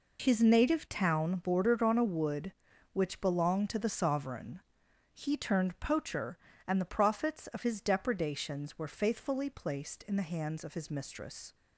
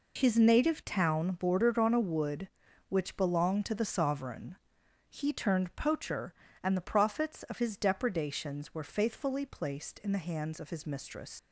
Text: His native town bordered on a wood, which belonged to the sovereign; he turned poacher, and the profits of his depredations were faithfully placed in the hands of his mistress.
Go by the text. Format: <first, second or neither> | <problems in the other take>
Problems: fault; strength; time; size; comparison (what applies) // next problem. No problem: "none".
first | leaves "mistress" unfinished; at 11.3 s; 110 ms